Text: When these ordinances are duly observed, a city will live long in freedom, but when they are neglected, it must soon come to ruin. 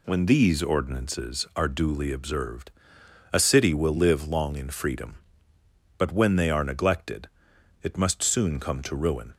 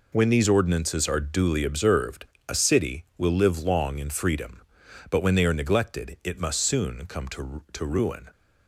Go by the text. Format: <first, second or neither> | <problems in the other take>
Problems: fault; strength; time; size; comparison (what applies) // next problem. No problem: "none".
first | says "to" twice; at 7.7 s